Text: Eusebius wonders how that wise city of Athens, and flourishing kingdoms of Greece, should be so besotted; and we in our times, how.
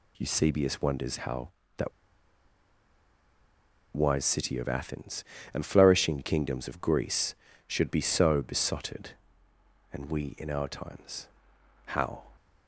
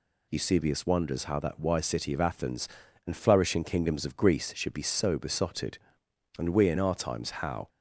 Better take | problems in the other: second | pauses between "that" and "wise"; strong; at 1.9 s; 2.0 s long

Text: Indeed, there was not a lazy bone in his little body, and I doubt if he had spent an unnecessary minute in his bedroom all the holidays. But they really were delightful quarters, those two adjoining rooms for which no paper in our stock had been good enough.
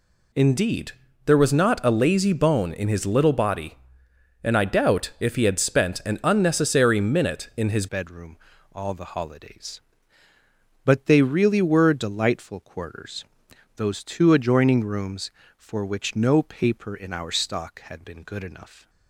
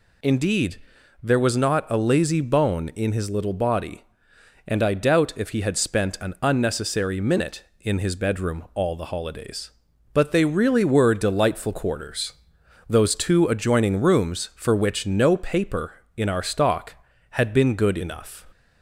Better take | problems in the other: second | changes voice at "bedroom"; from 7.8 s on; 11.0 s long // pauses between "bedroom" and "all"; at 8.3 s; 0.38 s long

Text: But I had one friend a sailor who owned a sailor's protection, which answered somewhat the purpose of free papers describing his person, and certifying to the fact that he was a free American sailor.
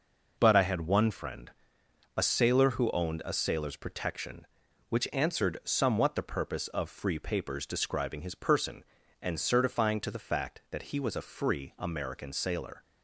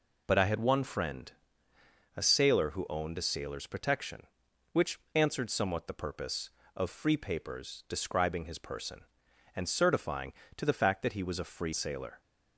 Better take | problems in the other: first | pauses between "friend" and "a"; noticeable; at 1.3 s; 0.84 s long; noticeable in the first // pauses between "which" and "answered"; slight; at 4.9 s; 0.16 s long // skips "American"; at 11.7 s

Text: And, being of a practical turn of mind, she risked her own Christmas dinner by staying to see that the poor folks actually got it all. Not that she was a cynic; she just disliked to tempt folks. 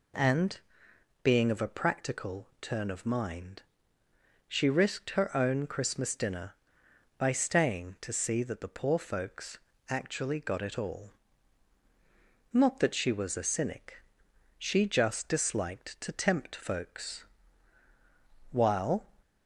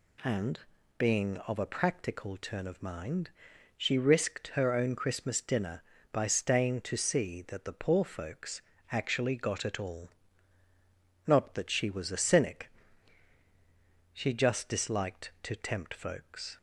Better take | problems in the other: second | pauses between "folks" and "actually"; slight; at 9.5 s; 0.32 s long; slight in the second // goes on to say "While"; from 18.5 s on; 0.52 s long

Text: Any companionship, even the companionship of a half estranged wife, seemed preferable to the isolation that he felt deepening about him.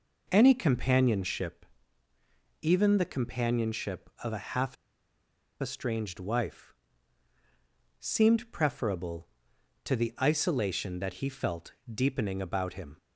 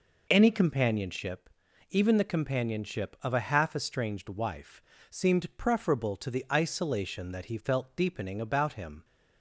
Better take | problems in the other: second | pauses between "half" and "estranged"; noticeable; at 4.7 s; 0.85 s long // pauses between "felt" and "deepening"; slight; at 11.7 s; 0.20 s long

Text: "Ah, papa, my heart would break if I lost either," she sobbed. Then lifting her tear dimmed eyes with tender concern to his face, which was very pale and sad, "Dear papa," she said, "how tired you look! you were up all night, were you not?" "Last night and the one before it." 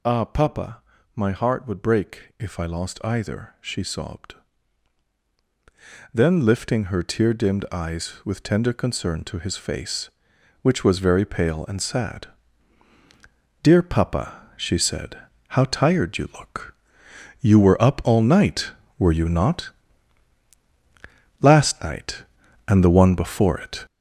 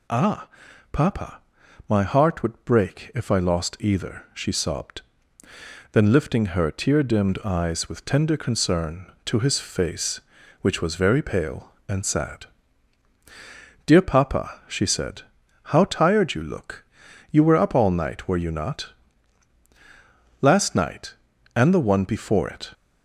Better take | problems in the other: second | gets louder; strong; throughout; 8 dB

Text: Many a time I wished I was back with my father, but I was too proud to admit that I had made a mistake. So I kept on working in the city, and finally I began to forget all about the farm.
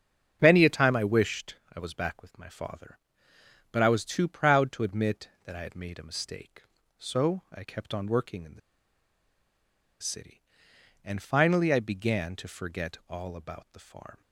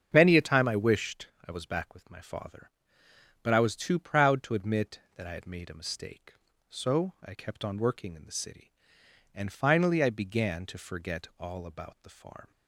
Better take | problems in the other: second | starts louder than the rest; strong; until 1.4 s; 7.5 dB; strong in the second // pauses between "wished" and "I"; slight; at 1.5 s; 0.18 s long; slight in the second // pauses between "the" and "city"; strong; at 8.5 s; 1.4 s long

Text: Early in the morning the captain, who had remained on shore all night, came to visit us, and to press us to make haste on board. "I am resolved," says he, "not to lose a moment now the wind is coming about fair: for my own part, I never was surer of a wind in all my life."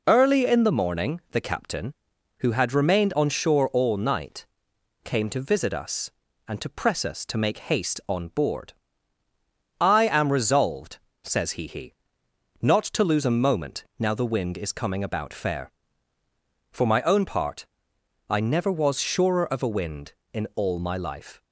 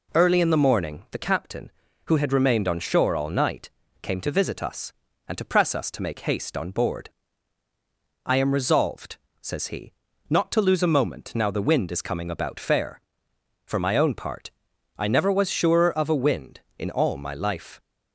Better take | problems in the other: second | says "he" twice; at 11.6 s

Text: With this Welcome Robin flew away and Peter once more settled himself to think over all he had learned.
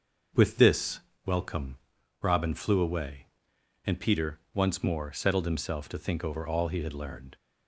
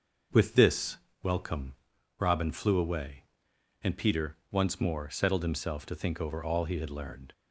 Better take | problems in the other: neither | starts louder than the rest; the same in both // pauses between "this" and "Welcome"; slight; the same in both // pauses between "Welcome" and "Robin"; noticeable; the same in both // pauses between "Peter" and "once"; slight; the same in both

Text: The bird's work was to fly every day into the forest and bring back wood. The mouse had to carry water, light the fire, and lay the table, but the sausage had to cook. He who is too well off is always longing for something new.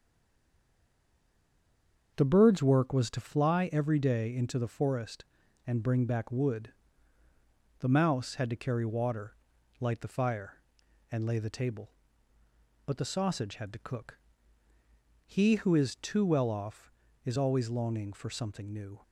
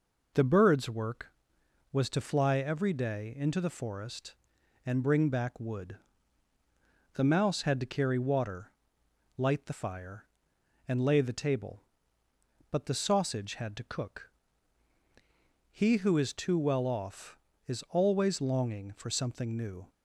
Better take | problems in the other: second | stays silent before the first word; until 2.1 s; 2.1 s long // starts louder than the rest; until 3.1 s; 7 dB

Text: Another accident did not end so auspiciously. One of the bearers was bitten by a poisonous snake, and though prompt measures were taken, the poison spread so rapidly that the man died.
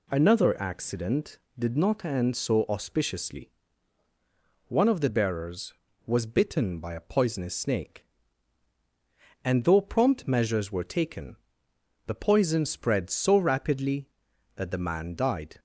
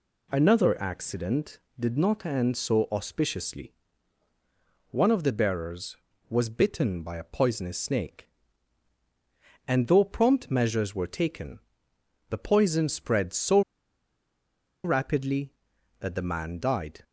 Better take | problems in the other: first | pauses between "so" and "rapidly"; at 13.6 s; 1.2 s long

